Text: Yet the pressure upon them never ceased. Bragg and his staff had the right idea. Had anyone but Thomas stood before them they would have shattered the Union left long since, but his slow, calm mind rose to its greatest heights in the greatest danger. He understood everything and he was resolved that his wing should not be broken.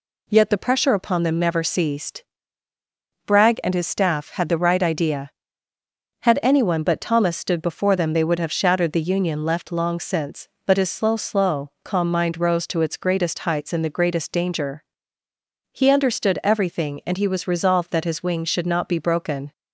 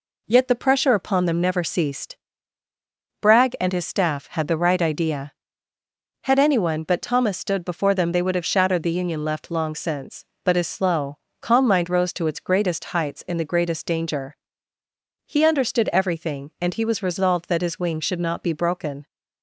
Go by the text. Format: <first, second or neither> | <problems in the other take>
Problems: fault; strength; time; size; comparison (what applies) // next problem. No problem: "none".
second | says "slow" twice; at 11.1 s